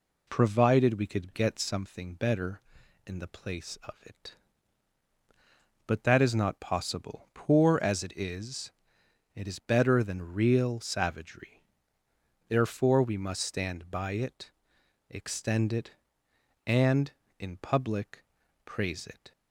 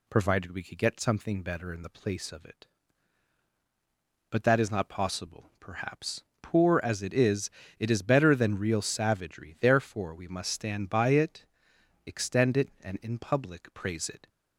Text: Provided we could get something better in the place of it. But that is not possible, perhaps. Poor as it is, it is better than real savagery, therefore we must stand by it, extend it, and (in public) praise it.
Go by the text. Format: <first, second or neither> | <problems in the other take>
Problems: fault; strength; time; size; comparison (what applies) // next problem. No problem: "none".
second | skips "perhaps"; at 7.3 s